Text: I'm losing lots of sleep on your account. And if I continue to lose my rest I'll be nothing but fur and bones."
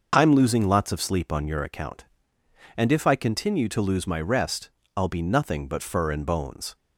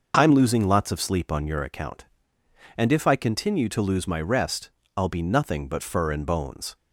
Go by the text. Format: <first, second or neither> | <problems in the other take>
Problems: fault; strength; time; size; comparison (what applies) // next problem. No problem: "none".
neither | pauses between "rest" and "I'll"; slight; the same in both